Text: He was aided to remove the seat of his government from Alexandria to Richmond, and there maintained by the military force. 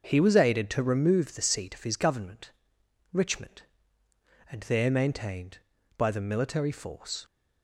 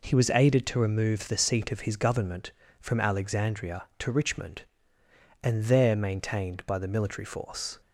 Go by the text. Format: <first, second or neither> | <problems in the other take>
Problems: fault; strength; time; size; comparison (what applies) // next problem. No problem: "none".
second | starts louder than the rest; noticeable; until 1.0 s; 6 dB // skips "from Alexandria to"; at 2.8 s